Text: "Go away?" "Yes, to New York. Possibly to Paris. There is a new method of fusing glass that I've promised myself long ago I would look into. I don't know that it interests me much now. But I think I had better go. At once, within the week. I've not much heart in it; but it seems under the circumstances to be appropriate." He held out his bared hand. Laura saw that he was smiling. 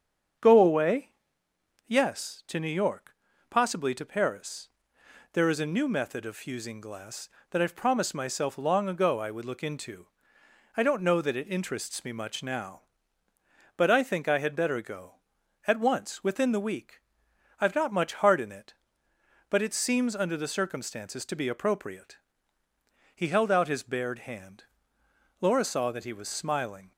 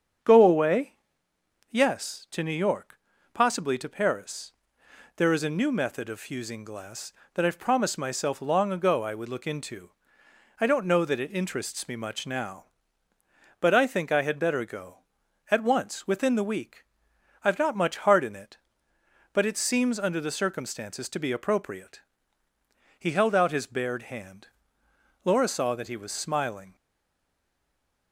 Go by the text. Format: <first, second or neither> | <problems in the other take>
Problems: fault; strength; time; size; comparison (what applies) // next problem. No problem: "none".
first | starts louder than the rest; strong; until 1.9 s; 7.5 dB; strong in the first // stays silent after the last word; noticeable; from 26.7 s on; 1.4 s long